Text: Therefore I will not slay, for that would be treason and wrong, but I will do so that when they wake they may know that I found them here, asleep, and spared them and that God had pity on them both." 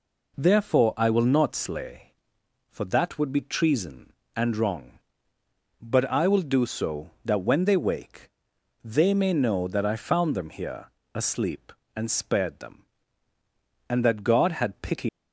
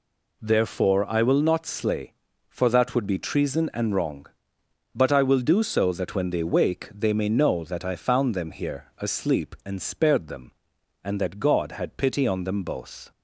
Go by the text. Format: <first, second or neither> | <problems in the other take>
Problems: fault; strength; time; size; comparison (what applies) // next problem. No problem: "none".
second | pauses between "wake" and "they"; noticeable; at 8.2 s; 0.54 s long // stops before "on them both"; at 15.0 s